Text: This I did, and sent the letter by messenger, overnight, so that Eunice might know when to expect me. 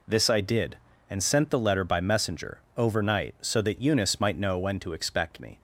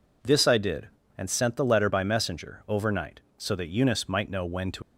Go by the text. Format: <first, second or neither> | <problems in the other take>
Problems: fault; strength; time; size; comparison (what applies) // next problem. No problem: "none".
first | stops before "expect me"; at 4.8 s